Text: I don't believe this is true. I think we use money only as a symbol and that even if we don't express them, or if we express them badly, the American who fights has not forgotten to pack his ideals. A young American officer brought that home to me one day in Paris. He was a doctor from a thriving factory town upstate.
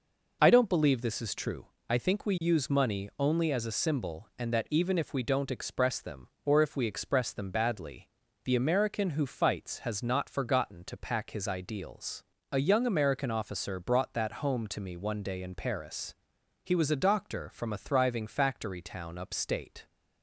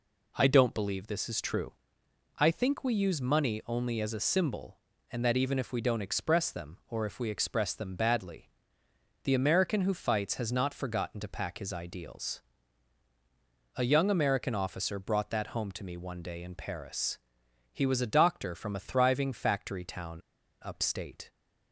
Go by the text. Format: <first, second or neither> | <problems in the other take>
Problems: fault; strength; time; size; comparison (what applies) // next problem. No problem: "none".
first | pauses between "town" and "upstate"; at 20.2 s; 0.45 s long